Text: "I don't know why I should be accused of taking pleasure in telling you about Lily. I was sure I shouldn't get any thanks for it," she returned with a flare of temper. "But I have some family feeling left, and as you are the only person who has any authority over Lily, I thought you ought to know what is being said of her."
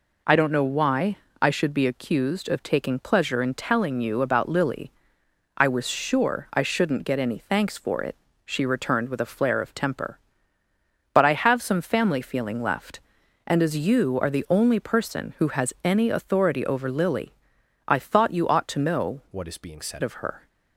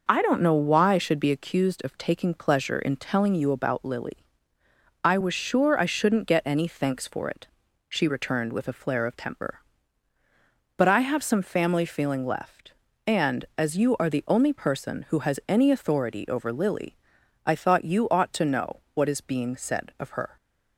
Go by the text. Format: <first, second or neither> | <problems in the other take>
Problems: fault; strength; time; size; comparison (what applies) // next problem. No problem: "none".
second | pauses between "why" and "I"; slight; at 1.1 s; 0.24 s long // changes voice from "what" to "said"; from 19.3 to 20.0 s; 0.7 s long